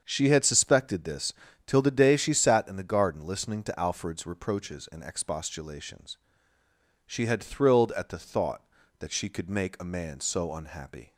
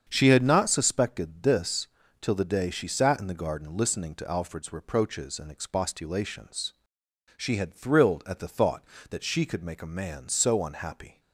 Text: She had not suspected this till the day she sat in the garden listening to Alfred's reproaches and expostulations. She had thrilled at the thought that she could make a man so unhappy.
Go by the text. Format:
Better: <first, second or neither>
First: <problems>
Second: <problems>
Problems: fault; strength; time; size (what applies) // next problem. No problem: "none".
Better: second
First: starts louder than the rest; until 1.0 s; 7 dB // skips "not"; at 0.4 s // pauses between "this" and "till"; slight; at 1.3 s; 0.34 s long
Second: starts louder than the rest; strong; until 1.1 s; 7.5 dB // pauses between "this" and "till"; slight; at 1.8 s; 0.34 s long